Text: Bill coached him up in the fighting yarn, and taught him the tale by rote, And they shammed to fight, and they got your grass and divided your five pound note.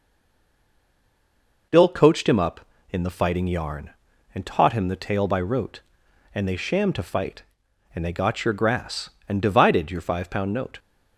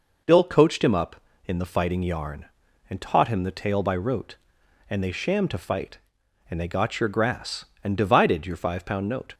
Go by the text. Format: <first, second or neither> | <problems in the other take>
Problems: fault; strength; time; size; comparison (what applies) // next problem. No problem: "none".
second | stays silent before the first word; noticeable; until 1.7 s; 1.7 s long